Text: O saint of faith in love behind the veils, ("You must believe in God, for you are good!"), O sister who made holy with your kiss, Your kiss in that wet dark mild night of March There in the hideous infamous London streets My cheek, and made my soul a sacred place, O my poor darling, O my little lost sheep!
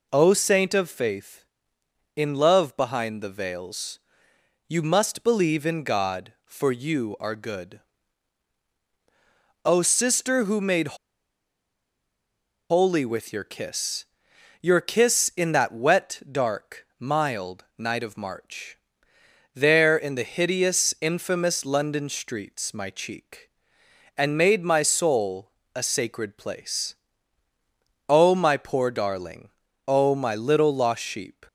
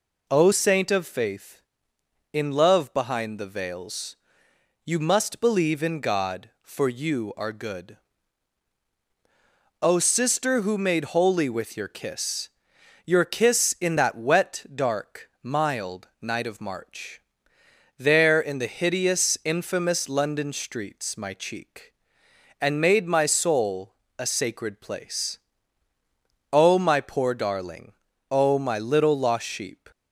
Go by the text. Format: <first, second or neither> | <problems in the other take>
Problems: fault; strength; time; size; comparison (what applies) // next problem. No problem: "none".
second | pauses between "made" and "holy"; strong; at 10.9 s; 1.7 s long // pauses between "March" and "There"; noticeable; at 18.7 s; 0.74 s long; noticeable in the second // pauses between "soul" and "a"; slight; at 25.4 s; 0.24 s long; slight in the second